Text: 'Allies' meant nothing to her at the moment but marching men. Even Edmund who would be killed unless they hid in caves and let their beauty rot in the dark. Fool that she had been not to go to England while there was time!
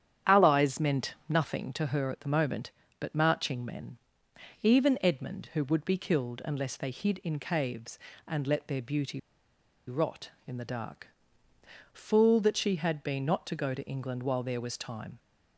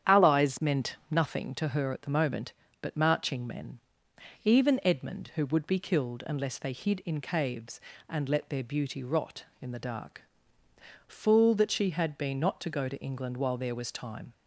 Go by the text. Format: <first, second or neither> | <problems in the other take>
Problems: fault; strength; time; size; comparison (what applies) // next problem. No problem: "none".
second | starts louder than the rest; strong; until 1.4 s; 9.5 dB; strong in the second // pauses between "meant" and "nothing"; slight; at 1.1 s; 0.16 s long; slight in the second // pauses between "beauty" and "rot"; noticeable; at 9.1 s; 0.68 s long